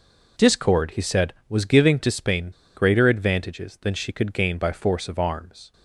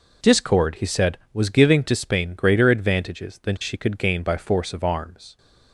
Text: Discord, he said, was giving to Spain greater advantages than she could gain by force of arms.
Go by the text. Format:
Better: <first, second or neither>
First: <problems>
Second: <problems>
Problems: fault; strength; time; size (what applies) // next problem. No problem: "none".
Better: second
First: pauses between "Spain" and "greater"; slight; at 2.5 s; 0.24 s long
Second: none